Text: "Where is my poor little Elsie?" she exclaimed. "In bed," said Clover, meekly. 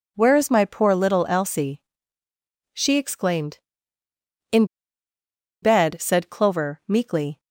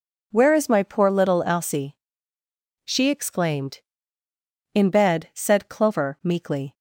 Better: second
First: pauses between "In" and "bed"; noticeable; at 4.6 s; 0.98 s long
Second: none

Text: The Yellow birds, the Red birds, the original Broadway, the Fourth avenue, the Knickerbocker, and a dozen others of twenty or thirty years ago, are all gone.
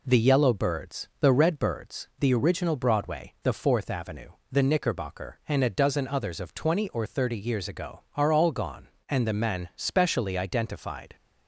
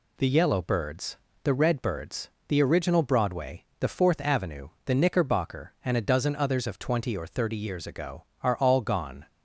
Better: second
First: goes on to say "And the men specially identified"; strong; from 9.0 s on; 2.0 s long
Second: none

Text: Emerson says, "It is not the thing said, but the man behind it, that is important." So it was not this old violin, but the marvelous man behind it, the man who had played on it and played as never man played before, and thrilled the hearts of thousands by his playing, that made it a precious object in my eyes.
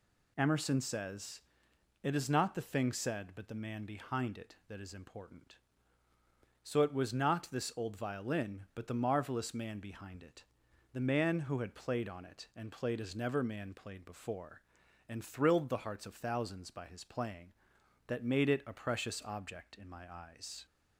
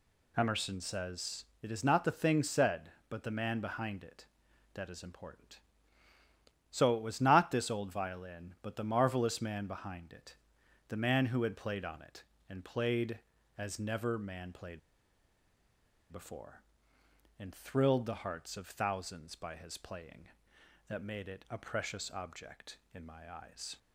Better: first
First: none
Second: pauses between "played" and "before"; strong; at 14.7 s; 1.3 s long

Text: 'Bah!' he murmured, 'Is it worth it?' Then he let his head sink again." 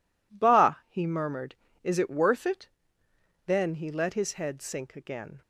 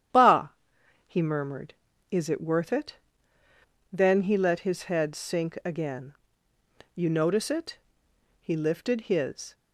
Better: first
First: none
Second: starts louder than the rest; strong; until 1.7 s; 10 dB // goes on to say "You notice it He lifted his"; strong; from 6.9 s on; 2.6 s long

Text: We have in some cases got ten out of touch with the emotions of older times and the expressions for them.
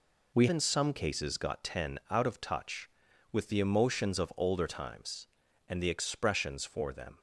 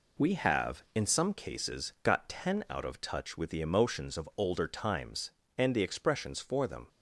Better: second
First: skips "have"; at 0.4 s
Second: none

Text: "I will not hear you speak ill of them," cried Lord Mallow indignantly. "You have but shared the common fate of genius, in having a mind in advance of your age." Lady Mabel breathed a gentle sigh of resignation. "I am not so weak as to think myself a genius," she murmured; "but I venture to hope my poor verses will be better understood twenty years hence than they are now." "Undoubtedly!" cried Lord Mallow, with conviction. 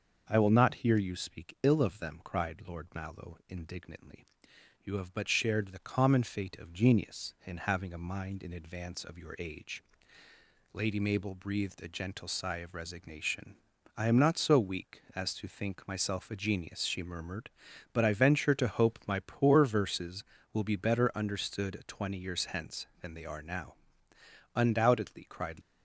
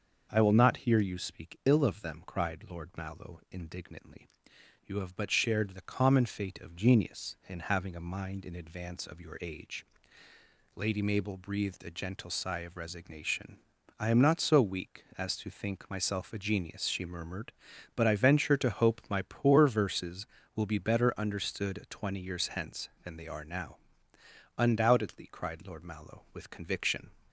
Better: second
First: starts louder than the rest; until 1.2 s; 6.5 dB // stops before "Lord Mallow with conviction"; at 25.6 s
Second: starts louder than the rest; until 1.3 s; 6.5 dB

